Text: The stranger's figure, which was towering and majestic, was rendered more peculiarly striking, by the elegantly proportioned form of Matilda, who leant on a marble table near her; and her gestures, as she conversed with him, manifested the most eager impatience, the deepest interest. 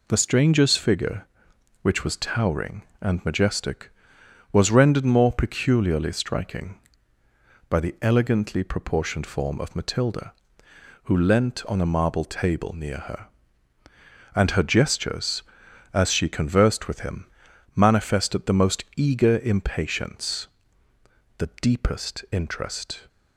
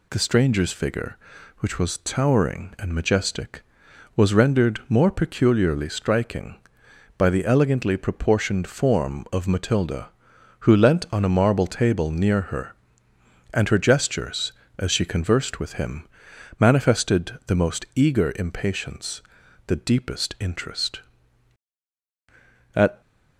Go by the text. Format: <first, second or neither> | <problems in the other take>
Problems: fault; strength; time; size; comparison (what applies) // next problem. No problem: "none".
first | goes on to say "At"; slight; from 22.7 s on; 0.24 s long